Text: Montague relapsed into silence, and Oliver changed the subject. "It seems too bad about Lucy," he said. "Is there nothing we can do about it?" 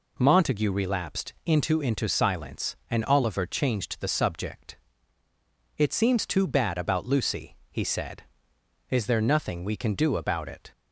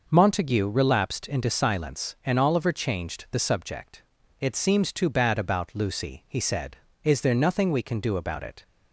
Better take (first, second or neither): second